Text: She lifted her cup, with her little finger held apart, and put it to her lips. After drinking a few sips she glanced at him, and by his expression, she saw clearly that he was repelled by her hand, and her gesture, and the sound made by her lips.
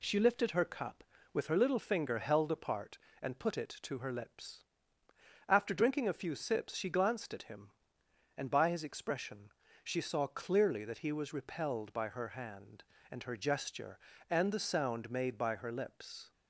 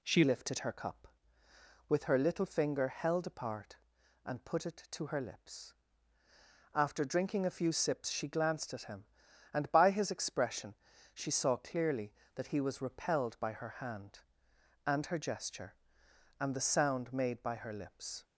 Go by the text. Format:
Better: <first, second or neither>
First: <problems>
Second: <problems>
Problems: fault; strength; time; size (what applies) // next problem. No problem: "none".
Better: first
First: none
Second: changes voice at "lifted"; from 0.2 s on; 18.0 s long